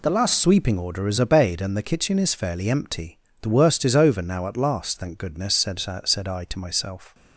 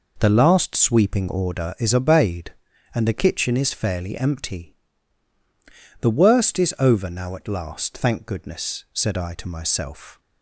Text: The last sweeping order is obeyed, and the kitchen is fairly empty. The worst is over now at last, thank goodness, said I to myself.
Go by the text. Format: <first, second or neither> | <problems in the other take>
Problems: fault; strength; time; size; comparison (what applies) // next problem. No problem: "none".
second | says "said" twice; at 6.0 s